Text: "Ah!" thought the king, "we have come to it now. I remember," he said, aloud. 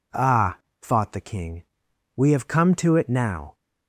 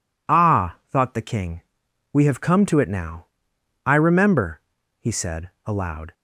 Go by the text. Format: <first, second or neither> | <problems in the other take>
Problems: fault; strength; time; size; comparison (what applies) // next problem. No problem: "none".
second | stops before "I remember he said aloud"; at 3.5 s